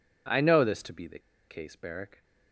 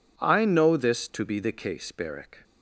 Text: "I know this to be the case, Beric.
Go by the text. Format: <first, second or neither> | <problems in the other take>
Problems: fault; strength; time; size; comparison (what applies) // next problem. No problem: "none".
second | pauses between "the" and "case"; slight; at 1.1 s; 0.28 s long